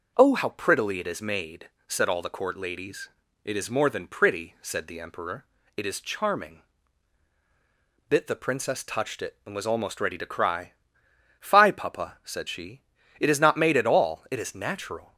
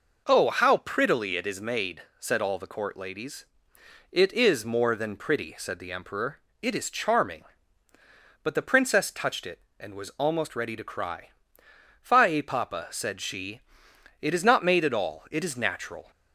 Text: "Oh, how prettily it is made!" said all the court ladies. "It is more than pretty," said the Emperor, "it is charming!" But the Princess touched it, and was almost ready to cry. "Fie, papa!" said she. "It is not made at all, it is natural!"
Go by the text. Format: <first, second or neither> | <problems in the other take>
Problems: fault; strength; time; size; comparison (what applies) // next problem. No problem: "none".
second | says "Bit" for "But"; at 8.0 s